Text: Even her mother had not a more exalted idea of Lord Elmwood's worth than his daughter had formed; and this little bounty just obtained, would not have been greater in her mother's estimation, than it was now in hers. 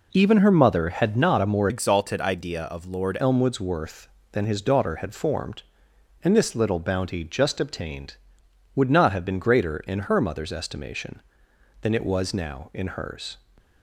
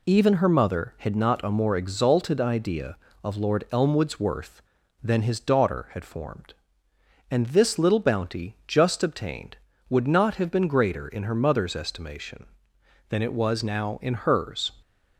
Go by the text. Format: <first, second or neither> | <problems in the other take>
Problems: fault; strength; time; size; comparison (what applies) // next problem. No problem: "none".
second | changes voice from "exalted" to "Lord"; from 1.6 to 3.1 s; 1.5 s long